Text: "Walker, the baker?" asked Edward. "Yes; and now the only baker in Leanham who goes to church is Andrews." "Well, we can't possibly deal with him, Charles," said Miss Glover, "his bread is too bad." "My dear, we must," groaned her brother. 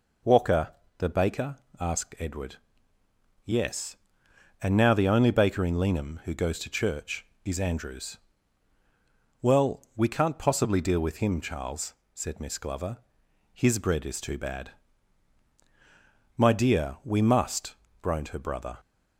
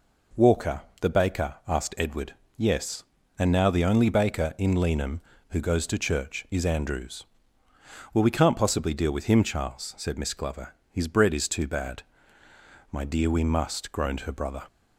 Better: neither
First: none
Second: none

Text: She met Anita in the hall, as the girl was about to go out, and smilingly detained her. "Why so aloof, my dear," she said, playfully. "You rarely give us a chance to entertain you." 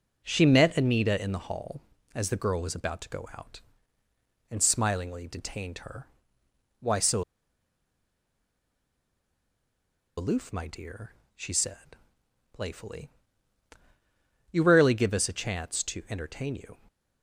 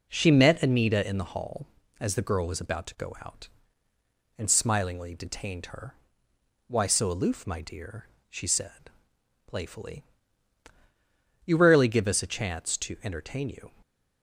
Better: second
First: pauses between "so" and "aloof"; strong; at 7.2 s; 2.9 s long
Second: none

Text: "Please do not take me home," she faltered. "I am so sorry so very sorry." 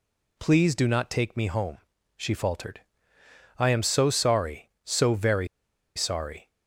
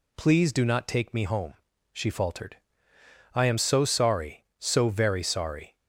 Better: second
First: pauses between "very" and "sorry"; noticeable; at 5.4 s; 0.48 s long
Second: none

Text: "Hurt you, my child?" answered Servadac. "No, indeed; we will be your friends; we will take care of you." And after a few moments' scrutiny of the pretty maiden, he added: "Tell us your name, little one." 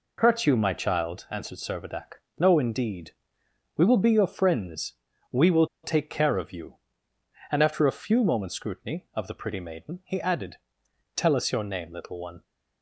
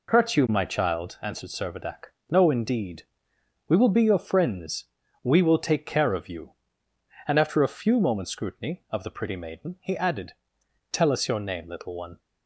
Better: second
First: pauses between "will" and "take"; slight; at 5.6 s; 0.18 s long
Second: none

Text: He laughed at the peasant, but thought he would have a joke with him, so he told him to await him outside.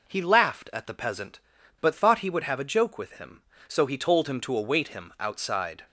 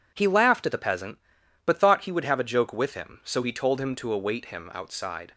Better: neither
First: none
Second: none

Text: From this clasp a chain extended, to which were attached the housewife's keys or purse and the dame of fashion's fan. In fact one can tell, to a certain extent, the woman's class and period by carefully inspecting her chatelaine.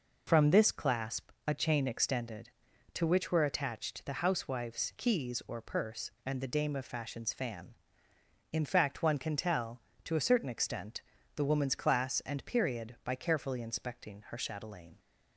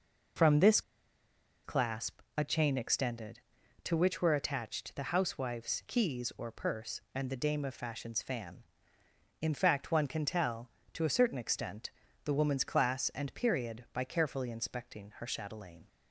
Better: first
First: pauses between "clasp" and "a"; slight; at 1.3 s; 0.16 s long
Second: pauses between "this" and "clasp"; noticeable; at 0.8 s; 0.83 s long // pauses between "clasp" and "a"; slight; at 2.2 s; 0.16 s long

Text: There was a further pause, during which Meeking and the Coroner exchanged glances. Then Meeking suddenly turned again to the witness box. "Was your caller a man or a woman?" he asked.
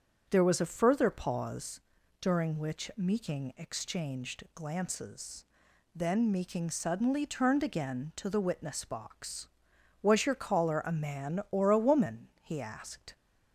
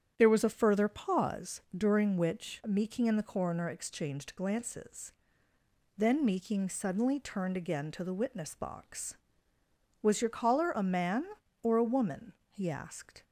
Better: second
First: starts louder than the rest; strong; until 1.2 s; 7.5 dB // skips "and the Coroner"; at 3.5 s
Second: starts louder than the rest; strong; until 1.1 s; 9 dB

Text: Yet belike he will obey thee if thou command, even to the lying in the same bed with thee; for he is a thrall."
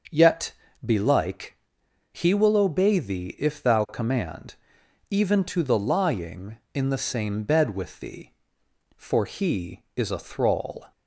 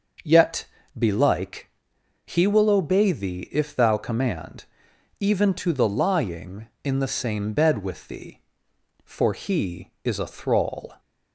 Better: neither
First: starts louder than the rest; noticeable; until 1.4 s; 6 dB // pauses between "Yet" and "belike"; slight; at 0.5 s; 0.32 s long // pauses between "belike" and "he"; noticeable; at 1.5 s; 0.56 s long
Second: starts louder than the rest; noticeable; until 1.5 s; 6 dB // pauses between "Yet" and "belike"; slight; at 0.6 s; 0.32 s long // pauses between "belike" and "he"; noticeable; at 1.6 s; 0.56 s long

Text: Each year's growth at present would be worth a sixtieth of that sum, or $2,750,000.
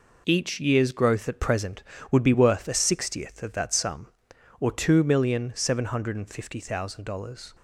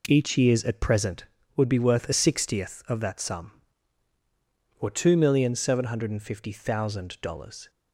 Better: first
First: none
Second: skips "growth"; at 0.6 s

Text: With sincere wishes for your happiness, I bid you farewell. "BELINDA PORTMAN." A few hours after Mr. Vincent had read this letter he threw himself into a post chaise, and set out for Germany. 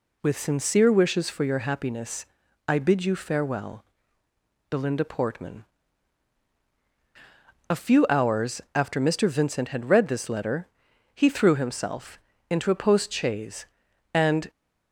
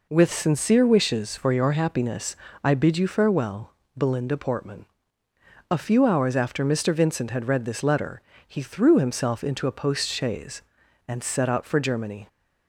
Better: second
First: pauses between "letter" and "he"; noticeable; at 10.6 s; 0.48 s long // pauses between "himself" and "into"; slight; at 12.1 s; 0.32 s long // stops before "set out for Germany"; at 14.4 s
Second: pauses between "letter" and "he"; slight; at 8.1 s; 0.26 s long

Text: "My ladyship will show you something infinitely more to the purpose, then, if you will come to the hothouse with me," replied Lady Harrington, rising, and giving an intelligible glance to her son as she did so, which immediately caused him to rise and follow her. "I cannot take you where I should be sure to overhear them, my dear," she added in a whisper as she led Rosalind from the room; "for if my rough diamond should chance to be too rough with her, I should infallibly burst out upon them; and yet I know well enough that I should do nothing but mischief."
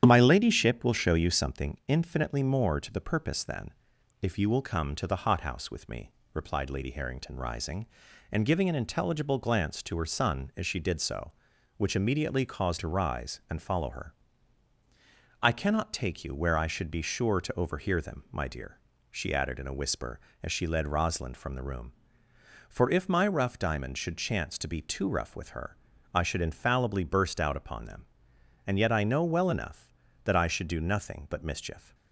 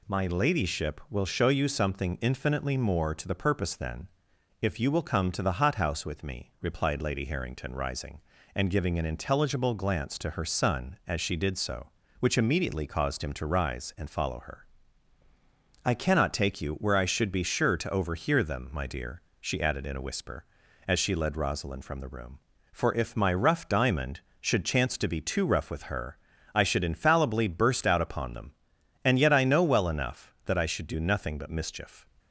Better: second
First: starts louder than the rest; strong; until 1.0 s; 9.5 dB // skips "him"; at 12.7 s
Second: none

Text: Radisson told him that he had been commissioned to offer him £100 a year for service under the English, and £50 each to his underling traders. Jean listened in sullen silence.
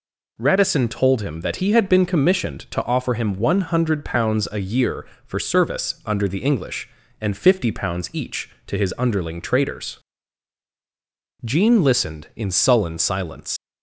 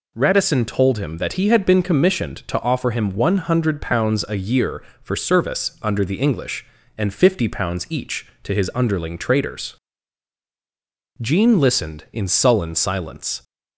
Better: second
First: leaves "silence" unfinished; at 13.5 s; 100 ms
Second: none

